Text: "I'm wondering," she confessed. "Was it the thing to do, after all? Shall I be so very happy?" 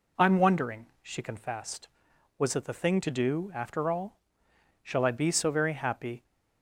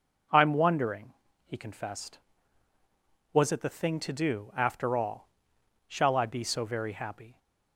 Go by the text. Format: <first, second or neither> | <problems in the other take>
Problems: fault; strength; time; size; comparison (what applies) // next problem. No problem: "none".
first | says "he" for "she"; at 1.4 s